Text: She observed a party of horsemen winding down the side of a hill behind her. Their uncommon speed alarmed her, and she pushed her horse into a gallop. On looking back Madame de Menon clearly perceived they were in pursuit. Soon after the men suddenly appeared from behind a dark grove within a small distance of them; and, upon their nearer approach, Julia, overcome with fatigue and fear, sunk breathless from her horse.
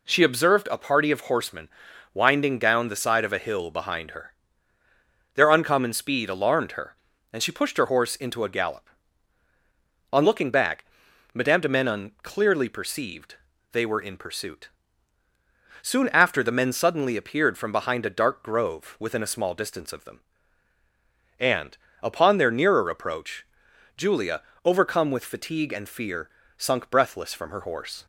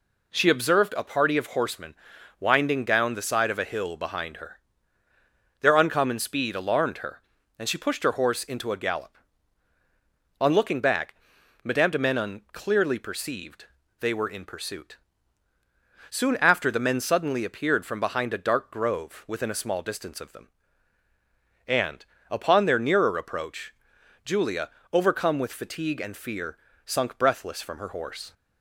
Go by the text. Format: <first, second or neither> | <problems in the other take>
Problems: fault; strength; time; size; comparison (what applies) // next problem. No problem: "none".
neither | pauses between "horsemen" and "winding"; noticeable; the same in both // pauses between "back" and "Madame"; noticeable; the same in both // pauses between "perceived" and "they"; slight; the same in both